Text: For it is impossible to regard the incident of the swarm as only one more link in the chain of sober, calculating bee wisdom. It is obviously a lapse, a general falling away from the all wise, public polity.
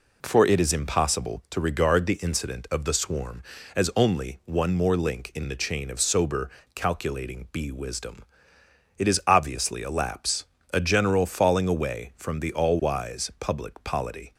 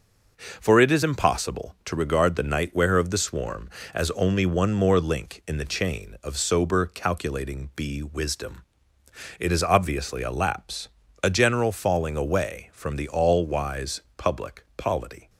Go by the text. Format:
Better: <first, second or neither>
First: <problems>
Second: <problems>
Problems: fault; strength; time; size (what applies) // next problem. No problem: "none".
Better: first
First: none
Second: starts louder than the rest; until 1.3 s; 6.5 dB // says "nightwear" for "incident"; at 2.4 s